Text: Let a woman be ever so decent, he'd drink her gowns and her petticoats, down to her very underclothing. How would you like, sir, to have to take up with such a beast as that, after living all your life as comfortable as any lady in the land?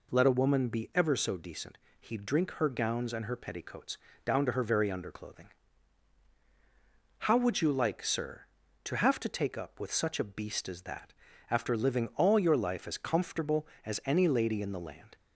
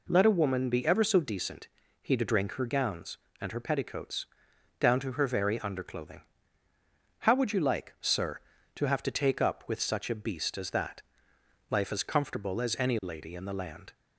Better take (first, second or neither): first